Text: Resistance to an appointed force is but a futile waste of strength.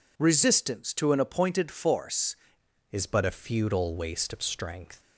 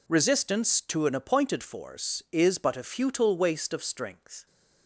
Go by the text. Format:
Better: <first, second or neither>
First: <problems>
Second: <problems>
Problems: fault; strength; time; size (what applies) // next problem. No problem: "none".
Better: second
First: changes voice at "is"; from 2.9 s on; 2.0 s long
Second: none